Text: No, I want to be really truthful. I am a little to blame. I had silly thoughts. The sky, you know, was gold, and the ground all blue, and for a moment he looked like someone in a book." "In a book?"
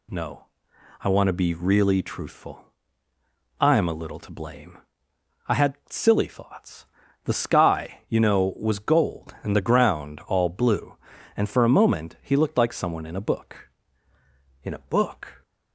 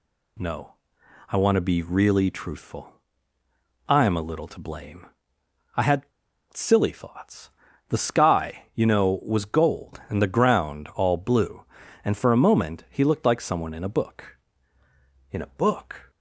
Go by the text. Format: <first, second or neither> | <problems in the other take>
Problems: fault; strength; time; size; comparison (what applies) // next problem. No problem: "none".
first | pauses between "had" and "silly"; noticeable; at 6.0 s; 0.46 s long